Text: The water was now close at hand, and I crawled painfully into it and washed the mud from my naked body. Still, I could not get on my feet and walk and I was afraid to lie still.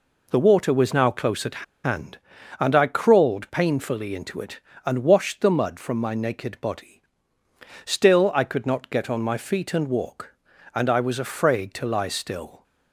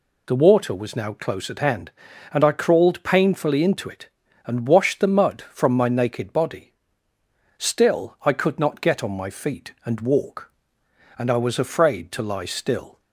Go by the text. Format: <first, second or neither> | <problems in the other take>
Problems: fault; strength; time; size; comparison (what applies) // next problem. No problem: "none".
second | pauses between "at" and "hand"; slight; at 1.6 s; 0.20 s long